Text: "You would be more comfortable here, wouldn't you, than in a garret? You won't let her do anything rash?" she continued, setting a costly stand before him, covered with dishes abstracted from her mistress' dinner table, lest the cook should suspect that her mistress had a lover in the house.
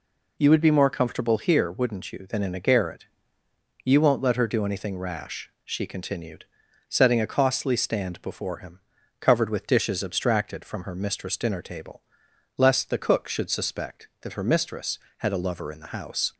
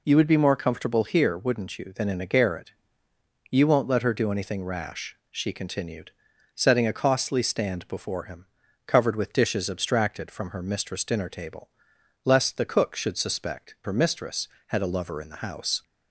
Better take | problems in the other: first | skips "that"; at 13.7 s

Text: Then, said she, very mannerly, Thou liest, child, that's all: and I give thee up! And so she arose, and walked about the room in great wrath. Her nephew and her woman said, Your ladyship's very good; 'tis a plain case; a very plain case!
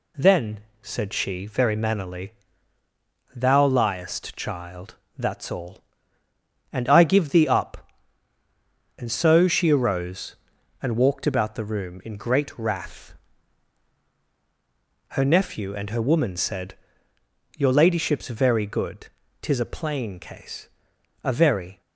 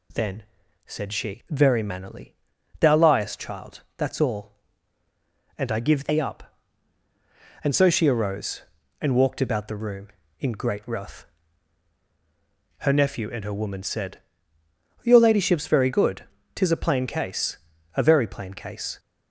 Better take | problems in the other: second | stops before "plain case"; at 21.8 s

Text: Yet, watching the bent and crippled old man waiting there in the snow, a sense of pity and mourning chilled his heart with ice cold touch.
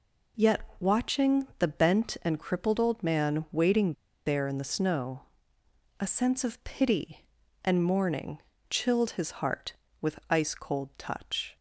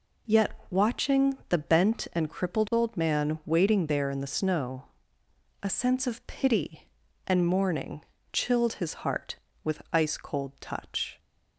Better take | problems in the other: second | pauses between "waiting" and "there"; slight; at 3.9 s; 0.33 s long // pauses between "mourning" and "chilled"; slight; at 8.3 s; 0.28 s long; slight in the second

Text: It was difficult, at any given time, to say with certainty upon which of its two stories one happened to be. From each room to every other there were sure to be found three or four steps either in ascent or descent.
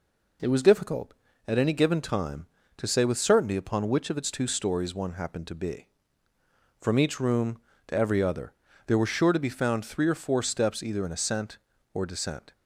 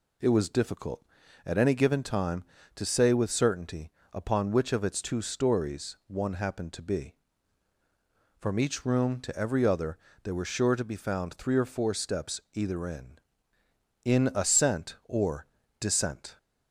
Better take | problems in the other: first | pauses between "certainty" and "upon"; slight; at 3.9 s; 0.22 s long // pauses between "other" and "there"; slight; at 9.9 s; 0.26 s long; slight in the first // says "in" twice; at 14.0 s // pauses between "or" and "descent"; slight; at 15.4 s; 0.36 s long

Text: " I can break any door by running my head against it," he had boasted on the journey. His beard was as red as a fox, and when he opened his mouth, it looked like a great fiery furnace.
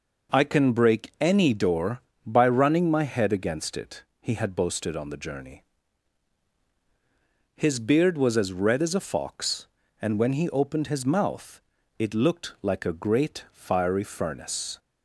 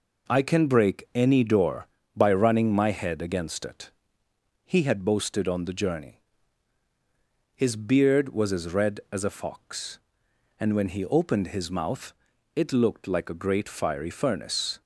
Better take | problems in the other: neither | none

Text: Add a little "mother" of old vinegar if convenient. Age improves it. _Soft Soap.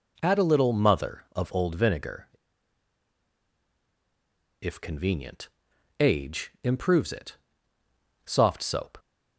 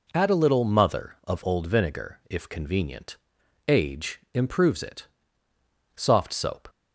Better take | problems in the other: second | pauses between "vinegar" and "if"; strong; at 2.2 s; 2.3 s long

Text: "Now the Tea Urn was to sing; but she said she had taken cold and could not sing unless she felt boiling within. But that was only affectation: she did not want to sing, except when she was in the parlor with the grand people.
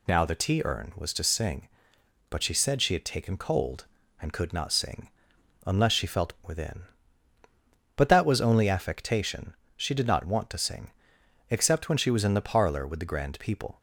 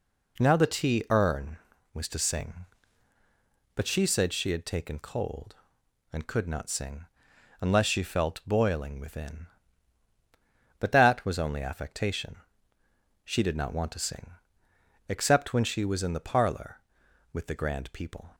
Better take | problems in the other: second | pauses between "sing" and "unless"; noticeable; at 5.0 s; 0.56 s long; noticeable in the second // skips "boiling"; at 6.3 s

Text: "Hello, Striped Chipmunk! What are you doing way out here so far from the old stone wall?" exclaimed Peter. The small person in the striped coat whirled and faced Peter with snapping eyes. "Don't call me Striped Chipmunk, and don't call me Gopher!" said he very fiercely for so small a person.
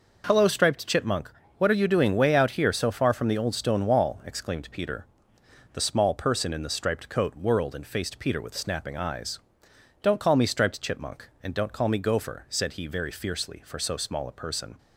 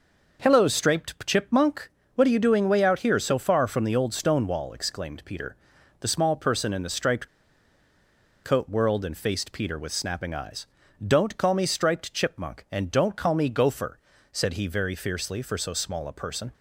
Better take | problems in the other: first | pauses between "striped" and "coat"; at 7.2 s; 1.1 s long

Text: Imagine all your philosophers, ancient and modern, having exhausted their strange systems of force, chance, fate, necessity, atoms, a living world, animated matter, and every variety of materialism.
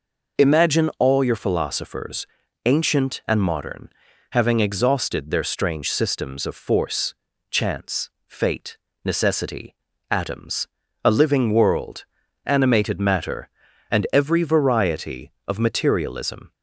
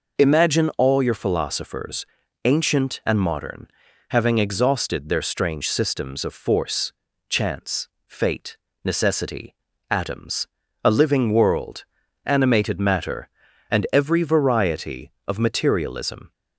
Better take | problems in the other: neither | none

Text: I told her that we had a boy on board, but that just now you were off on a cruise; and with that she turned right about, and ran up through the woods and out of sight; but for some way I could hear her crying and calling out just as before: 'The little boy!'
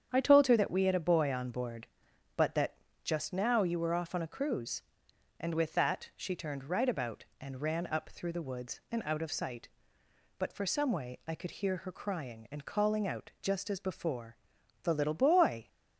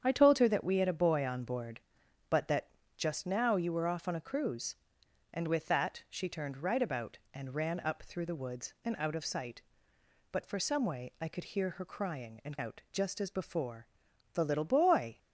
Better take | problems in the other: first | starts louder than the rest; strong; until 1.0 s; 8 dB; strong in the first // pauses between "that" and "just"; slight; at 2.6 s; 0.28 s long; slight in the first // skips "calling"; at 12.5 s

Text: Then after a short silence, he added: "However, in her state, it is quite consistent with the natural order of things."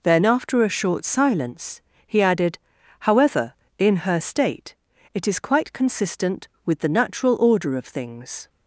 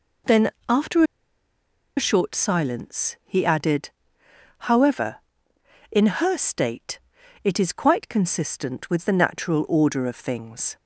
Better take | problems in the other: first | pauses between "Then" and "after"; slight; at 0.4 s; 0.18 s long // pauses between "after" and "a"; noticeable; at 1.0 s; 0.93 s long

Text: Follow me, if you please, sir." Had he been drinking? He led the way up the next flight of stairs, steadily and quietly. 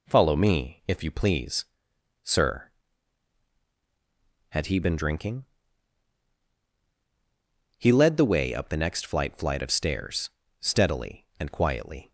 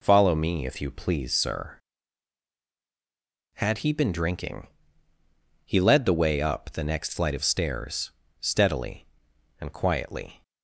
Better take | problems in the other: second | says "flight" twice; at 9.3 s

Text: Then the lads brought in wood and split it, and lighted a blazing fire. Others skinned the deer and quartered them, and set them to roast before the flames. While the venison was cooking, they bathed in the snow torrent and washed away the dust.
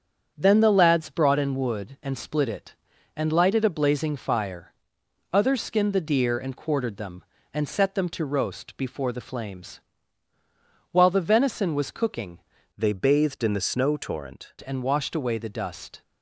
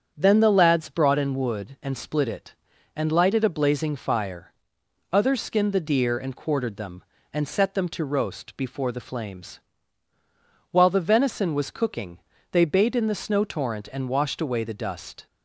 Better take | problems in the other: second | starts louder than the rest; strong; until 1.3 s; 7.5 dB; strong in the second // changes voice from "they" to "torrent"; from 12.7 to 14.5 s; 1.8 s long

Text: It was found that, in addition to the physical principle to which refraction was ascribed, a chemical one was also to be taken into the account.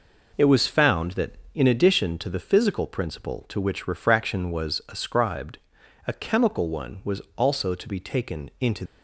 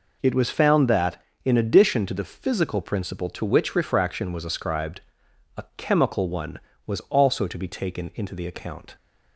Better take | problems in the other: second | stops before "the account"; at 8.8 s

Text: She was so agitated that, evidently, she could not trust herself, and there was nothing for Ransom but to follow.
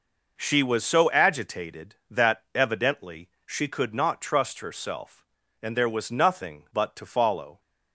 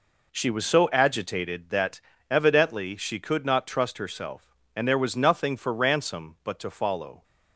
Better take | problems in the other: second | skips "for Ransom"; at 6.6 s

